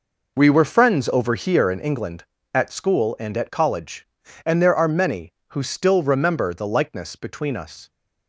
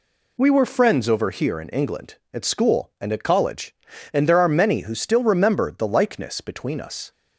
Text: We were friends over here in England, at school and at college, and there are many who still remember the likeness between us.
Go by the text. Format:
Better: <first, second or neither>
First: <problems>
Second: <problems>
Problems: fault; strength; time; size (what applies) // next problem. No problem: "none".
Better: second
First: starts louder than the rest; noticeable; until 2.0 s; 5 dB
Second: none